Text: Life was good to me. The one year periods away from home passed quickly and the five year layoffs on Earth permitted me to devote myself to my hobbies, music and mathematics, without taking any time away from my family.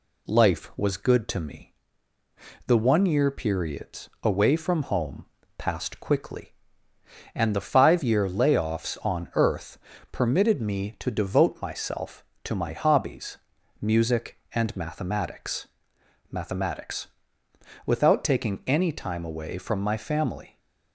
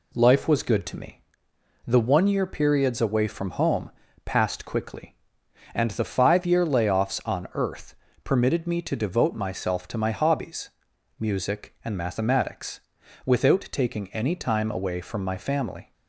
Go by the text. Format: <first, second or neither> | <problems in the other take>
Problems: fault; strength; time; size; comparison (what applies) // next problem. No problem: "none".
second | pauses between "home" and "passed"; slight; at 5.2 s; 0.30 s long; slight in the second // pauses between "Earth" and "permitted"; slight; at 9.7 s; 0.34 s long; slight in the second // says "mathematics" twice; at 16.3 s